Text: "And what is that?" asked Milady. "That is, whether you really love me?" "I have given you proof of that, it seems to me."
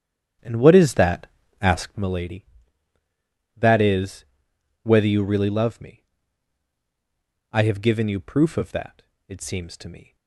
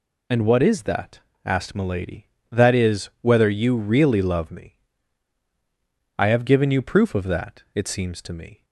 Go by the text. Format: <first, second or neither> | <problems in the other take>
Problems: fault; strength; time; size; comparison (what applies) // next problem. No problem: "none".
second | starts louder than the rest; strong; until 2.1 s; 9.5 dB